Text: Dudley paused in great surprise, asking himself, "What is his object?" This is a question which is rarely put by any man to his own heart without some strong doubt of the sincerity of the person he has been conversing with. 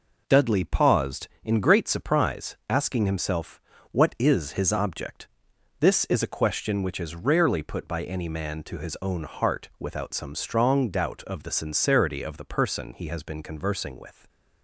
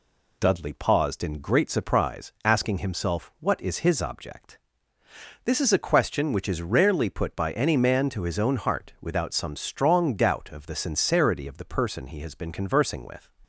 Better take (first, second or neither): neither